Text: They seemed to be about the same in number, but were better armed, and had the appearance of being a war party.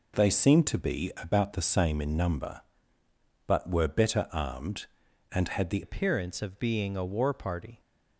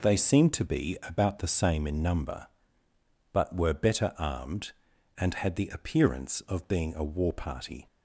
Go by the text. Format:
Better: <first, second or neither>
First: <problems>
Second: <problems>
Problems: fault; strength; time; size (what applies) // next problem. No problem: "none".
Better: second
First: changes voice at "appearance"; from 5.8 s on; 1.9 s long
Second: none